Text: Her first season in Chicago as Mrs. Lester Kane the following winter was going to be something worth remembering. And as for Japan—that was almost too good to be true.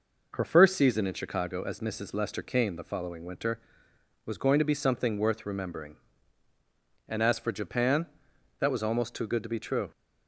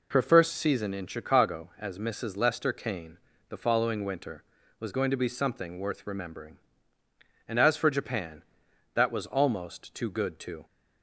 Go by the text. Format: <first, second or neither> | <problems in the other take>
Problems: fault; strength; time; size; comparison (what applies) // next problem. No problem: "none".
first | pauses between "Kane" and "the"; slight; at 3.1 s; 0.32 s long // stops before "be true"; at 10.6 s